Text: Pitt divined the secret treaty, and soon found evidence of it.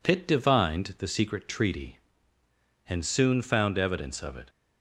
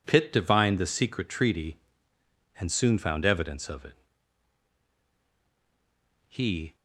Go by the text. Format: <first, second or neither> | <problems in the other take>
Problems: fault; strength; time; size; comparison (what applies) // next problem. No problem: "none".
first | goes on to say "He"; slight; from 6.2 s on; 0.48 s long